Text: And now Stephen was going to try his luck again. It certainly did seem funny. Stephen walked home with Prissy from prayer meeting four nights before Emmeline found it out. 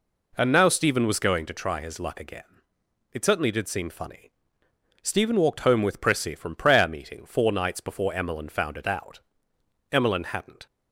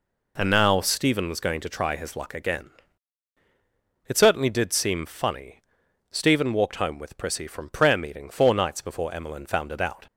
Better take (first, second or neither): second